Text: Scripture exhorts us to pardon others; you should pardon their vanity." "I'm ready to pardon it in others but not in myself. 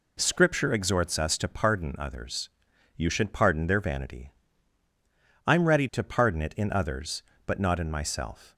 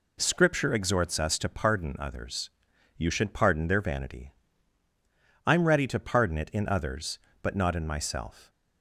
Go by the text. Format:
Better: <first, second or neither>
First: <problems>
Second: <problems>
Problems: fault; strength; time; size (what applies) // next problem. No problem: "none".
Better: neither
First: none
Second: none